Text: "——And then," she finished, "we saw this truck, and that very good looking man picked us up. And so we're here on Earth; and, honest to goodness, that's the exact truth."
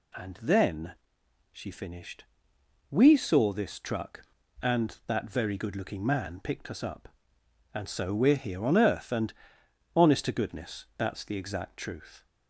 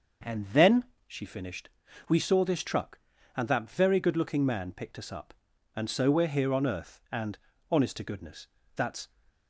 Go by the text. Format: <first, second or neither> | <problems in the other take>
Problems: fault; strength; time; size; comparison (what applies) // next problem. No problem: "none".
first | starts louder than the rest; until 1.5 s; 6 dB // stops before "the exact truth"; at 9.2 s